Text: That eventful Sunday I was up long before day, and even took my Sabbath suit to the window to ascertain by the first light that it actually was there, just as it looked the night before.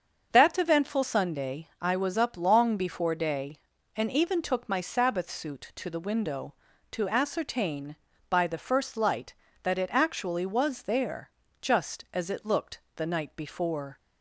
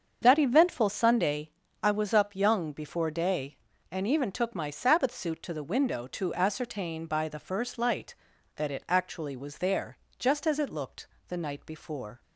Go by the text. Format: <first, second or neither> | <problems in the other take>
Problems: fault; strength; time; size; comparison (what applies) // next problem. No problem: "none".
first | starts louder than the rest; until 1.2 s; 7 dB; also in the first // pauses between "Sunday" and "I"; slight; at 1.4 s; 0.34 s long // says "young" for "long"; at 2.3 s // pauses between "looked" and "the"; slight; at 11.0 s; 0.20 s long; slight in the first